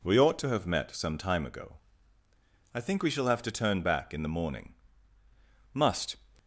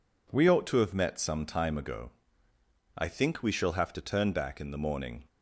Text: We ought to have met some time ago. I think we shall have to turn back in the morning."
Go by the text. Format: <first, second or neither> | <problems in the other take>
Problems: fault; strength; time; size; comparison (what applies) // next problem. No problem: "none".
second | goes on to say "Must"; slight; from 5.7 s on; 0.42 s long